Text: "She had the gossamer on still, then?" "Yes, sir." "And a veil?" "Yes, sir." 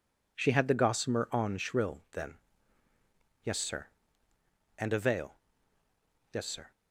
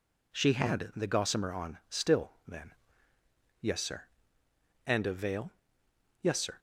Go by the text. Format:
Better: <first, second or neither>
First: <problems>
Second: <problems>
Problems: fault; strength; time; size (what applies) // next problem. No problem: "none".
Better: second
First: says "shrill" for "still"; at 1.5 s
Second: none